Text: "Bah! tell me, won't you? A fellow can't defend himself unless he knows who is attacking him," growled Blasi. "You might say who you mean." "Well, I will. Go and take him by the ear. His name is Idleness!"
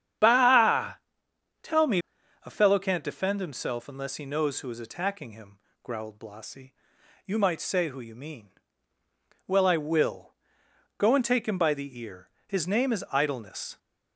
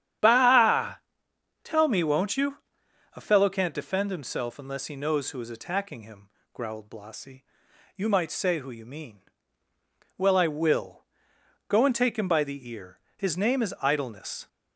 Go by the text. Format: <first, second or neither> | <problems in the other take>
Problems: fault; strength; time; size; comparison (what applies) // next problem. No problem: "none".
second | starts louder than the rest; strong; until 1.8 s; 9 dB; strong in the second // skips "won't you"; at 2.2 s